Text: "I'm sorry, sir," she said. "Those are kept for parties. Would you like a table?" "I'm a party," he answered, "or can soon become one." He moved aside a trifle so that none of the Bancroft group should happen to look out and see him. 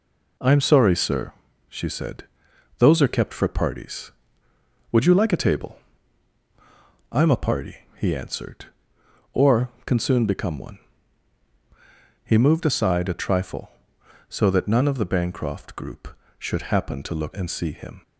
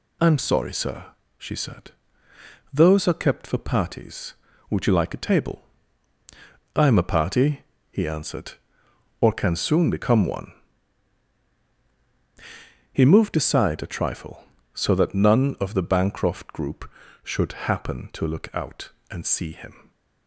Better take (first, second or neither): second